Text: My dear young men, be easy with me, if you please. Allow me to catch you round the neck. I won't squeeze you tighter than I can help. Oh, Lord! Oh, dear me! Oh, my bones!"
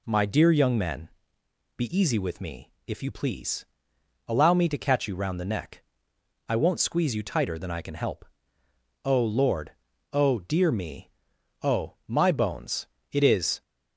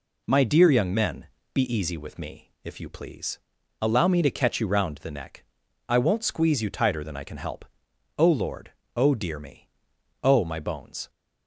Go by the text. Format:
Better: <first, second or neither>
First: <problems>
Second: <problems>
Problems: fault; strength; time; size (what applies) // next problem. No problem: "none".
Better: second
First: goes on to say "It is"; slight; from 13.1 s on; 0.48 s long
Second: none